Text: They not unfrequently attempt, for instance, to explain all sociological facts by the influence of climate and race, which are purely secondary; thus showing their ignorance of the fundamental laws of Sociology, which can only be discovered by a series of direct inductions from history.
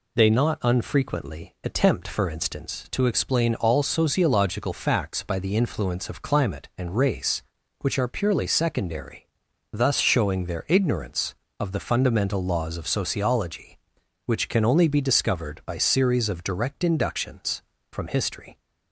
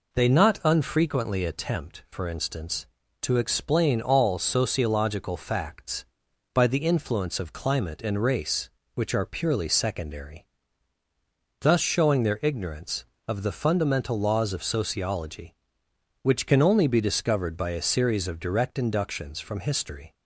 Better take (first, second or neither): second